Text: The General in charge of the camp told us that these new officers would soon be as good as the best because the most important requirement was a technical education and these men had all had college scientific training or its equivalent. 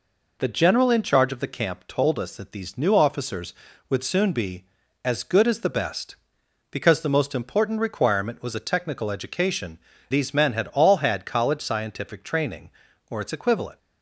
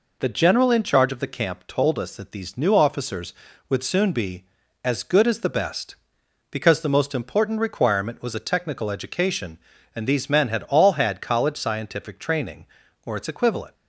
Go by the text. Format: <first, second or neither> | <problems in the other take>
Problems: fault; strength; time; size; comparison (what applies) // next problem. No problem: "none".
second | skips "and"; at 9.9 s